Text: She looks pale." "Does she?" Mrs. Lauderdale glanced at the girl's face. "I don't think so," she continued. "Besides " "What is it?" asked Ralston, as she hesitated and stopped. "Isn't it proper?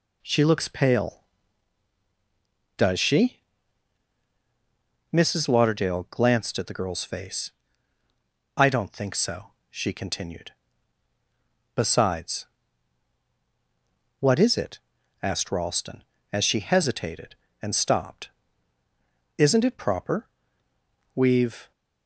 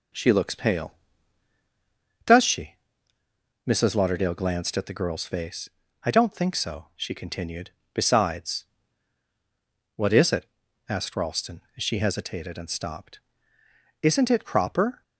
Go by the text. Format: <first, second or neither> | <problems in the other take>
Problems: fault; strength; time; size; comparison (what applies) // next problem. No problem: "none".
second | goes on to say "We've"; from 21.1 s on; 0.56 s long